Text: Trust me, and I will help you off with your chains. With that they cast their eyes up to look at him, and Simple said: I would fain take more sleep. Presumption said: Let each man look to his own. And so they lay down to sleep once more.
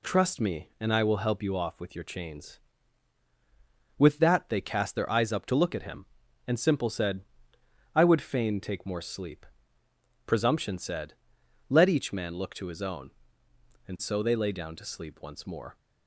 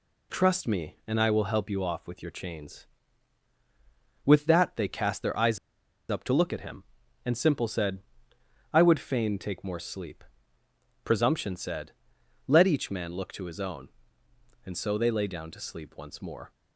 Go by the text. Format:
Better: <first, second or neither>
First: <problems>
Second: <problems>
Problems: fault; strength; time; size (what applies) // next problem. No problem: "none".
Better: first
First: none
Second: pauses between "eyes" and "up"; noticeable; at 5.5 s; 0.51 s long